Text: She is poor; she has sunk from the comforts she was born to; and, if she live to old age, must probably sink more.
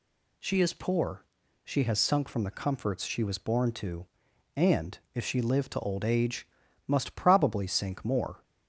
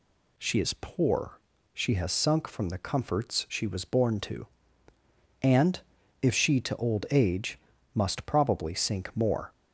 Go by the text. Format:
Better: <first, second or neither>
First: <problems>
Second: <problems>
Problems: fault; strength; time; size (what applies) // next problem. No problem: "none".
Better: first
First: none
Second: skips "live"; at 6.5 s